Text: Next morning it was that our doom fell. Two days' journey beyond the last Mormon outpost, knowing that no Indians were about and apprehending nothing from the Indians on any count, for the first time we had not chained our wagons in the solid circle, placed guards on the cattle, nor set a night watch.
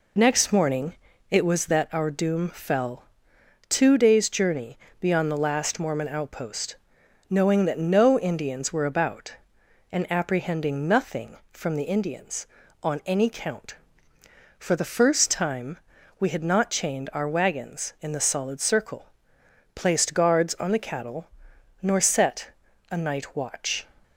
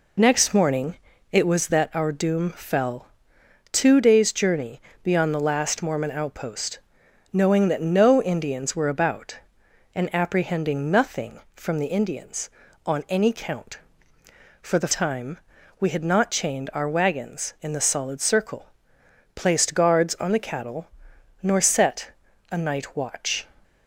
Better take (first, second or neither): first